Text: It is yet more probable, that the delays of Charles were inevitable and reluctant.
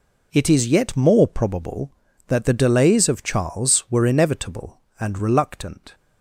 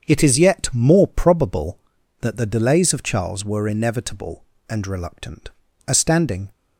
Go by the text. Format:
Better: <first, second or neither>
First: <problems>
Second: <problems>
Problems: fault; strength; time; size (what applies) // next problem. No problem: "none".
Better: first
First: none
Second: starts louder than the rest; strong; until 1.1 s; 7 dB // goes on to say "A standing"; noticeable; from 5.8 s on; 0.64 s long